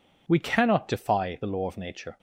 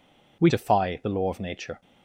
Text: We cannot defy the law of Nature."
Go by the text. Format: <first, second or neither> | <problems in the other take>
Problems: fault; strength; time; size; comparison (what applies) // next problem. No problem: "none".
first | skips "cannot"; at 0.4 s